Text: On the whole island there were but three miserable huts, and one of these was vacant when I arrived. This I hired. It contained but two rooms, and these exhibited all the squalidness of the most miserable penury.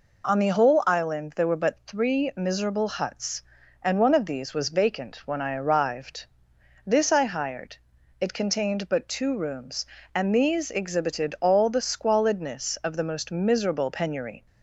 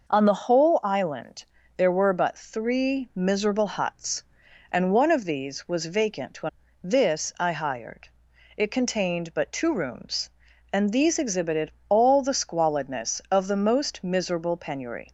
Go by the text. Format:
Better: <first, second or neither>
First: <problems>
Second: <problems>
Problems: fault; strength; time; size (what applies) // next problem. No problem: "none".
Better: first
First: none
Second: pauses between "island" and "there"; slight; at 1.4 s; 0.34 s long // skips "I arrived"; at 6.6 s // pauses between "exhibited" and "all"; slight; at 11.6 s; 0.18 s long